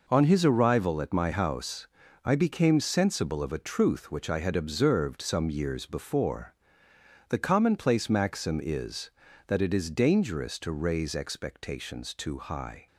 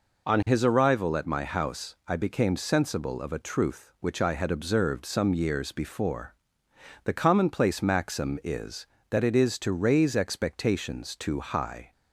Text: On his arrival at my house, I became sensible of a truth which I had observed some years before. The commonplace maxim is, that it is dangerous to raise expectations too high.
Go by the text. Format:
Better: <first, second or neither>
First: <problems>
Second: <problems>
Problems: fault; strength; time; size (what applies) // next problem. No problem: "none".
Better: first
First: none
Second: skips "dangerous"; at 9.5 s